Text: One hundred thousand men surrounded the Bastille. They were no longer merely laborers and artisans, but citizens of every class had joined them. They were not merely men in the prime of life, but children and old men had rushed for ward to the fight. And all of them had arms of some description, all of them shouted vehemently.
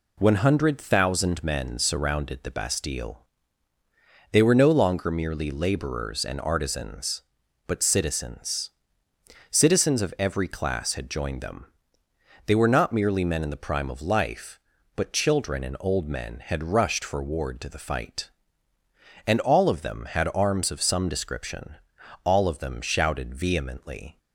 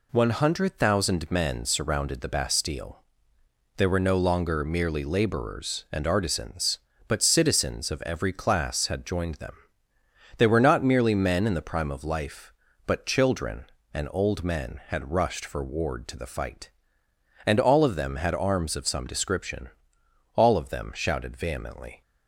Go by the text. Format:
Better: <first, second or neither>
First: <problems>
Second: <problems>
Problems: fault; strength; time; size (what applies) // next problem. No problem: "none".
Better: second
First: says "citizens" twice; at 9.5 s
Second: none